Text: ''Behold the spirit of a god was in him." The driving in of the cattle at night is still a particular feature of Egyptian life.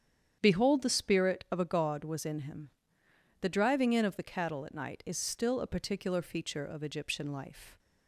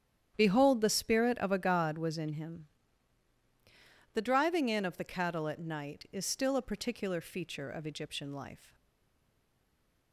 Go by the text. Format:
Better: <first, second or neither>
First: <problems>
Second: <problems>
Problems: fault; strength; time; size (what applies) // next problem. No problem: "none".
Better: first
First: starts louder than the rest; strong; until 1.4 s; 8.5 dB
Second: starts louder than the rest; strong; until 1.3 s; 9.5 dB // stays silent after the last word; noticeable; from 8.7 s on; 1.4 s long